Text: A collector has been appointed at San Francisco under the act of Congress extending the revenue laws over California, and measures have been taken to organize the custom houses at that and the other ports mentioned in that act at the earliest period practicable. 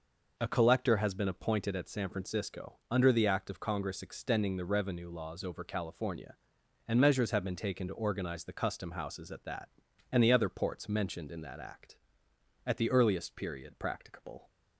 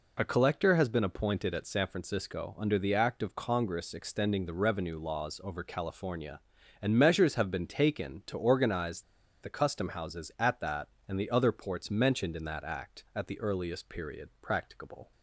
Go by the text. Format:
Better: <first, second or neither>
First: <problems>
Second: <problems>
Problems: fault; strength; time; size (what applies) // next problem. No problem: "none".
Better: first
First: none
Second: pauses between "organize" and "the"; at 9.0 s; 0.40 s long